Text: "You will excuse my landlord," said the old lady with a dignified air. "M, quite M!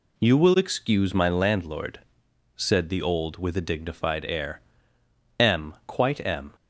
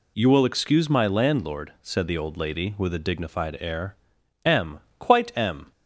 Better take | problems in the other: second | skips "lady"; at 3.3 s

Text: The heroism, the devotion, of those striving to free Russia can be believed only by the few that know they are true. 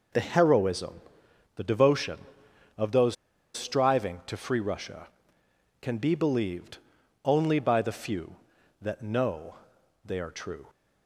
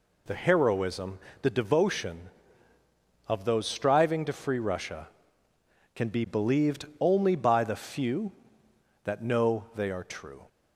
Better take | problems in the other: second | pauses between "those" and "striving"; at 3.1 s; 0.39 s long // pauses between "believed" and "only"; at 6.7 s; 0.44 s long // pauses between "know" and "they"; noticeable; at 9.5 s; 0.48 s long

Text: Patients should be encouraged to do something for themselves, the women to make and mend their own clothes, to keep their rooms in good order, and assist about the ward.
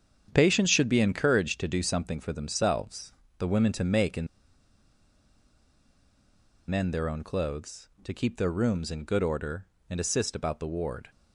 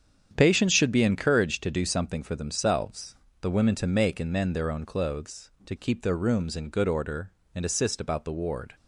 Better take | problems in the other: second | starts louder than the rest; strong; until 1.3 s; 8 dB; strong in the second // pauses between "and" and "mend"; strong; at 4.2 s; 2.4 s long

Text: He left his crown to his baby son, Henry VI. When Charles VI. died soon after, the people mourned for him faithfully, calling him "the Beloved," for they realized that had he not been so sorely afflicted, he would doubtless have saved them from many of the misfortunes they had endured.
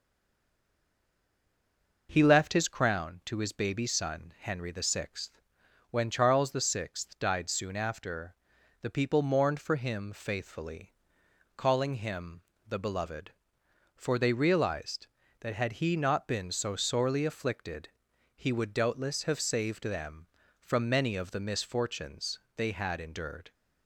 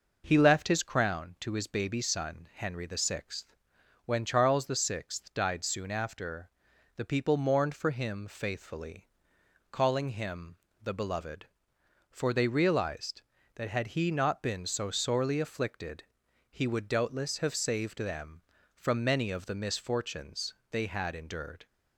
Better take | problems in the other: second | stays silent before the first word; noticeable; until 2.0 s; 2.0 s long // pauses between "him" and "the"; slight; at 12.4 s; 0.24 s long; slight in the second // pauses between "misfortunes" and "they"; slight; at 22.4 s; 0.16 s long; slight in the second

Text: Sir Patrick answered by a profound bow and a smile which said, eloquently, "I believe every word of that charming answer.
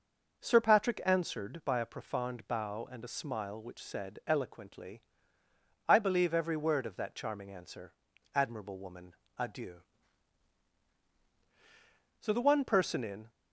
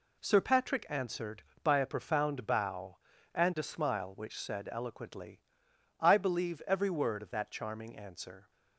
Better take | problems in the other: second | goes on to say "Admirable woman adieu So the one person in"; strong; from 8.3 s on; 4.9 s long

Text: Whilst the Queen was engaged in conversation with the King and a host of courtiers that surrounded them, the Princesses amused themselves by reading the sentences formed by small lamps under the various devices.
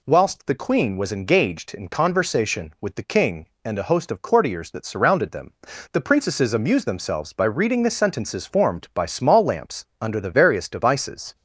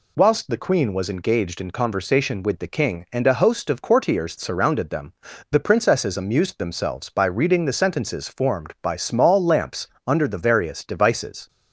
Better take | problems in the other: first | skips "that"; at 4.3 s // pauses between "lamps" and "under"; slight; at 9.8 s; 0.18 s long; slight in the first

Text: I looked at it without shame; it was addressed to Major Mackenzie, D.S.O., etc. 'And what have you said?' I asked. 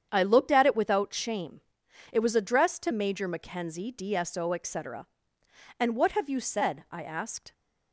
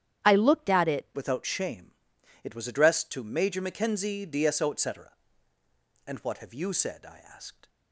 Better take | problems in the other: first | starts louder than the rest; strong; until 1.3 s; 10 dB; strong in the first // changes voice at "without"; from 1.1 s on; 6.5 s long

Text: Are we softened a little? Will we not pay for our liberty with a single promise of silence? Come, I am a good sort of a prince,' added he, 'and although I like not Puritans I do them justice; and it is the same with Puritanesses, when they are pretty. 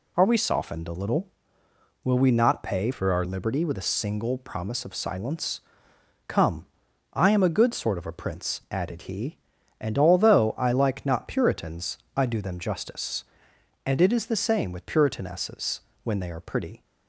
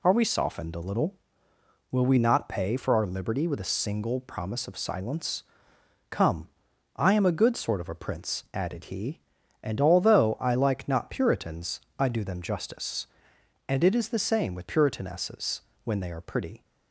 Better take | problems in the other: second | changes voice from "for" to "our"; from 2.9 to 3.2 s; 0.3 s long // pauses between "Puritans" and "I"; slight; at 11.9 s; 0.18 s long; slight in the second

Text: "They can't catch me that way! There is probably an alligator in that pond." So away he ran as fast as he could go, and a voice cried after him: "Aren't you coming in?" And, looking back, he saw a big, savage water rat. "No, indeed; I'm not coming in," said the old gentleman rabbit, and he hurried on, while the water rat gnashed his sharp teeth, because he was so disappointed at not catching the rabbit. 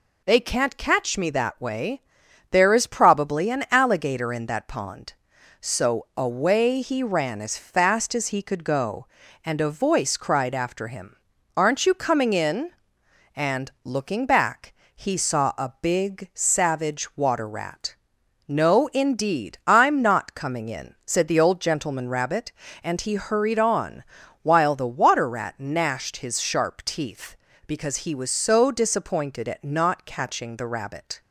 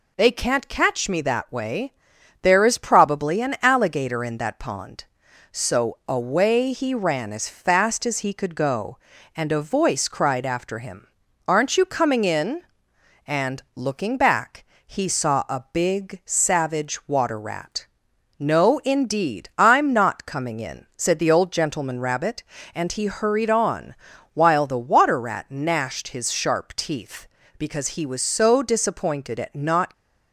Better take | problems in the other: first | stops before "catching the rabbit"; at 29.9 s

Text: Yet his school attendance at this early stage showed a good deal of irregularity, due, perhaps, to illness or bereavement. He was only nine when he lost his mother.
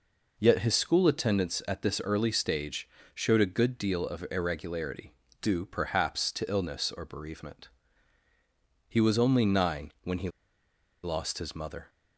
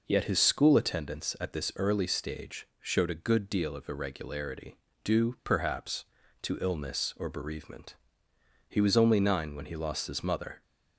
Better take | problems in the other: second | pauses between "stage" and "showed"; slight; at 2.8 s; 0.28 s long // pauses between "he" and "lost"; noticeable; at 10.2 s; 0.74 s long

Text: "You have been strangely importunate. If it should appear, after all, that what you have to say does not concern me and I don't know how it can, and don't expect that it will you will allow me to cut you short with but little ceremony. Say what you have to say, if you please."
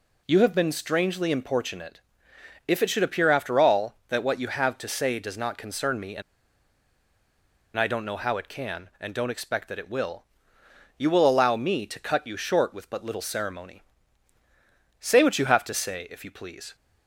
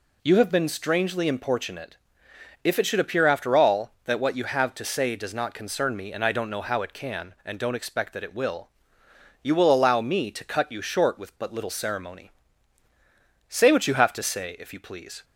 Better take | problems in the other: second | pauses between "and" and "I"; strong; at 6.2 s; 1.5 s long // pauses between "will" and "you"; noticeable; at 10.2 s; 0.74 s long; noticeable in the second

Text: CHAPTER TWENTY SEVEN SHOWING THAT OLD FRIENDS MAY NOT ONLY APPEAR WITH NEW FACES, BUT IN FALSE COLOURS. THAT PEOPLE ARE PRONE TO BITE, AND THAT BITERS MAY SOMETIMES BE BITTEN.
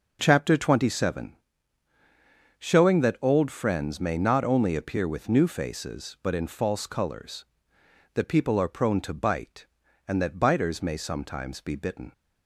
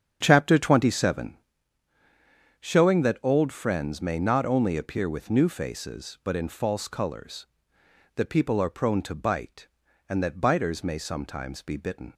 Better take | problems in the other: first | starts louder than the rest; strong; until 1.8 s; 8 dB // pauses between "SEVEN" and "SHOWING"; at 1.3 s; 1.2 s long; also in the first

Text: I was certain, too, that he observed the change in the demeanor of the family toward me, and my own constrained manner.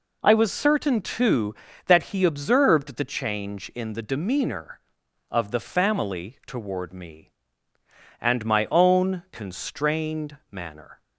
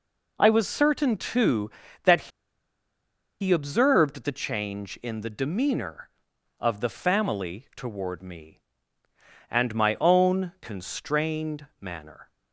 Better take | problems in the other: first | pauses between "that" and "he"; at 2.2 s; 1.1 s long

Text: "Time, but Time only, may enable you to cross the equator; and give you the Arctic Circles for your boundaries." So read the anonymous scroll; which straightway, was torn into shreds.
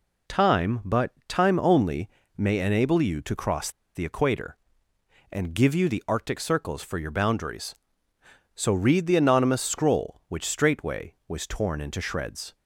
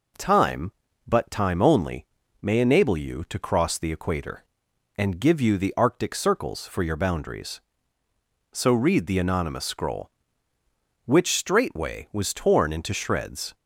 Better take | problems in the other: second | pauses between "but" and "Time"; slight; at 1.1 s; 0.16 s long // pauses between "cross" and "the"; slight; at 3.7 s; 0.24 s long

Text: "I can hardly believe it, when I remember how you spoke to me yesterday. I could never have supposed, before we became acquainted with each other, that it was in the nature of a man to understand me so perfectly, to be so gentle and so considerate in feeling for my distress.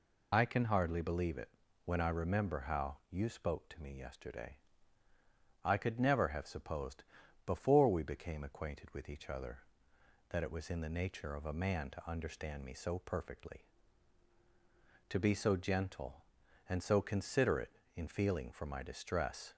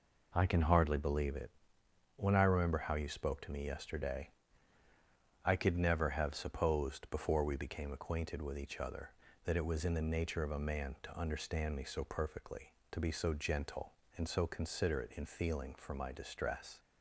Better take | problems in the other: second | loses the start of "I"; at 0.3 s; 75 ms

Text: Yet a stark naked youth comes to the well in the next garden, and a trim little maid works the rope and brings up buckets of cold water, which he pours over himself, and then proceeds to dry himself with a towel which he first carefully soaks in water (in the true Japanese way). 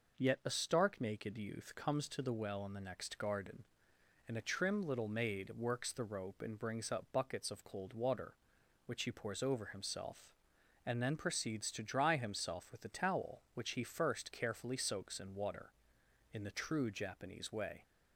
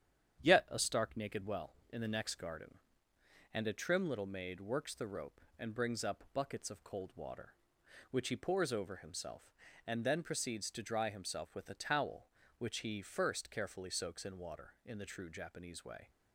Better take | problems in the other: first | starts louder than the rest; strong; until 1.4 s; 9 dB // skips "youth comes to the"; at 1.4 s

